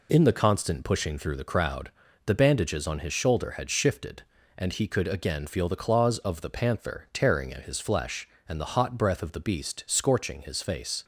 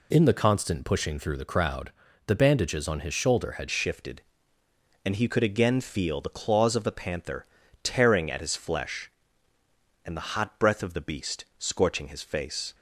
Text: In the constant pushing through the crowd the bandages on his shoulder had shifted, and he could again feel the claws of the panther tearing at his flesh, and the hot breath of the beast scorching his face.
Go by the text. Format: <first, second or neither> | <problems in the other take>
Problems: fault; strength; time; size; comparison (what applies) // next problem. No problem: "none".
first | pauses between "crowd" and "the"; slight; at 1.8 s; 0.36 s long; slight in the first // changes voice at "shifted"; from 3.7 s on; 9.0 s long // pauses between "panther" and "tearing"; slight; at 7.4 s; 0.36 s long